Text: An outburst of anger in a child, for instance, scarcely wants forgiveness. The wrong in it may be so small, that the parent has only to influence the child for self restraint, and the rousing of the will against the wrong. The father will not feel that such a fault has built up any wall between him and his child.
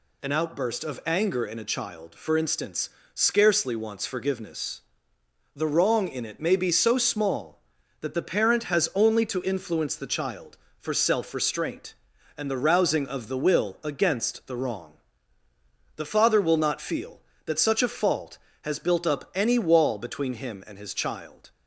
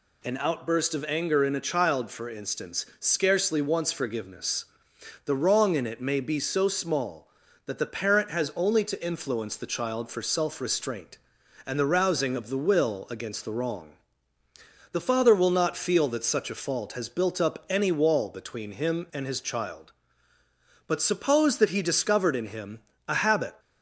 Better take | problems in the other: first | goes on to say "But suppose that he discovered in him a habit"; strong; from 20.8 s on; 2.7 s long

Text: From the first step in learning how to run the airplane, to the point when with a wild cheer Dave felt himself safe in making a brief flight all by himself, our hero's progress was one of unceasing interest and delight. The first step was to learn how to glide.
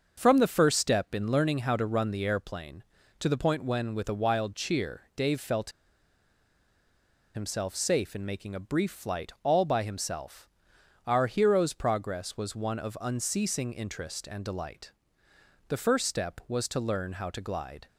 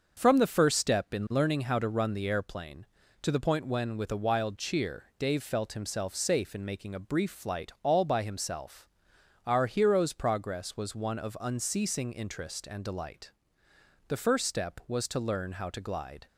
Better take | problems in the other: second | starts louder than the rest; until 1.1 s; 6.5 dB; also in the second // pauses between "felt" and "himself"; strong; at 5.7 s; 1.6 s long

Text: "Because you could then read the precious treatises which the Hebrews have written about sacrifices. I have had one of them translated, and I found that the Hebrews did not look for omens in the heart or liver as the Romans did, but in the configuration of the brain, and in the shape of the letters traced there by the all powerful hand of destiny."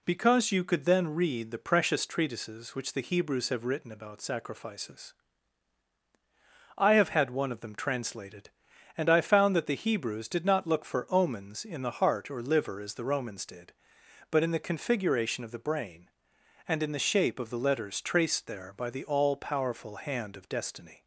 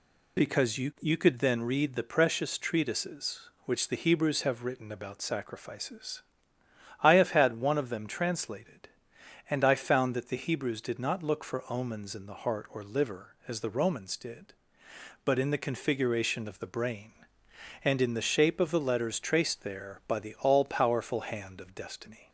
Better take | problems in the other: first | says "you" twice; at 0.9 s

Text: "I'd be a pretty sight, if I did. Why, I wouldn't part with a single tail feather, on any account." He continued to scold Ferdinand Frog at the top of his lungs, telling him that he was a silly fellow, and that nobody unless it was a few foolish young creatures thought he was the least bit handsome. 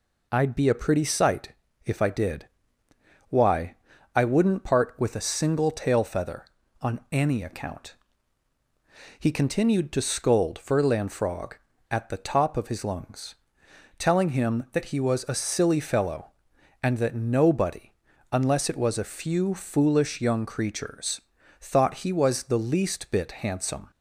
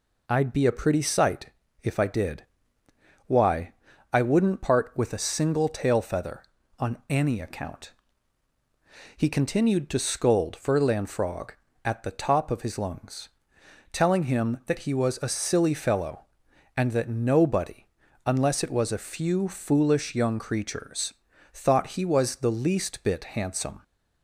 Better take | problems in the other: neither | pauses between "nobody" and "unless"; the same in both // pauses between "creatures" and "thought"; the same in both

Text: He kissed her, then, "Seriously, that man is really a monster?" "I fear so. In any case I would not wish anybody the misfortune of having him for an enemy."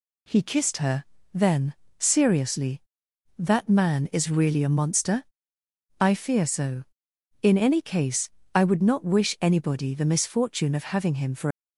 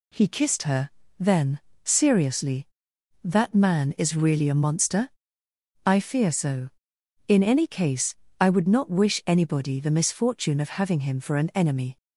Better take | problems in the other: second | pauses between "case" and "I"; slight; at 8.2 s; 0.24 s long; slight in the second // stops before "an enemy"; at 11.5 s

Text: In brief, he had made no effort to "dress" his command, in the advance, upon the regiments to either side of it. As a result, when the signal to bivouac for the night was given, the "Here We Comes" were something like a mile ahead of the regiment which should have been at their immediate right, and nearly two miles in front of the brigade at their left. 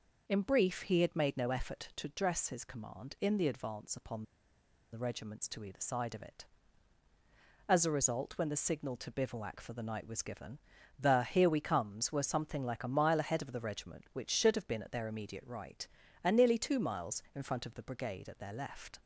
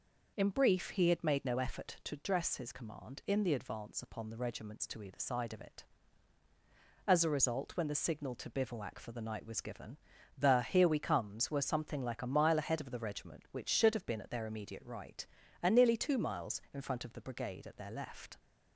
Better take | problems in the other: second | pauses between "upon" and "the"; noticeable; at 4.2 s; 0.68 s long

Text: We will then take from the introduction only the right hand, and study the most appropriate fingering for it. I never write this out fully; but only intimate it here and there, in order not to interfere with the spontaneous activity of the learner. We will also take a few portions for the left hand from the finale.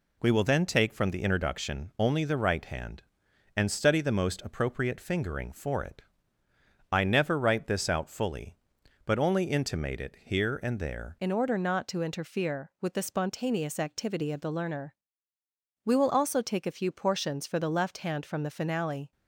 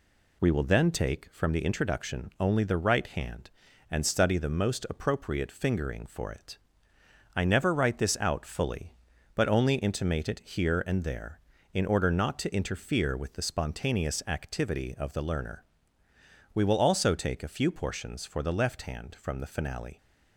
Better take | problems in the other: second | changes voice at "in"; from 11.1 s on; 8.0 s long

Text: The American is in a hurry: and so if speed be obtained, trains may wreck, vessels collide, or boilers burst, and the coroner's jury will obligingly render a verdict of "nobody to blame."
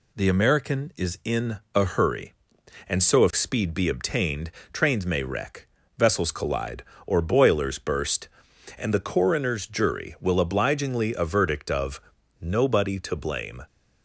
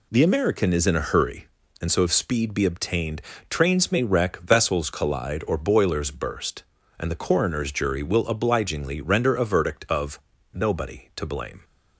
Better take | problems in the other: second | pauses between "in" and "a"; slight; at 1.5 s; 0.18 s long // skips "render"; at 11.1 s // pauses between "of" and "nobody"; at 11.9 s; 0.42 s long; slight in the second

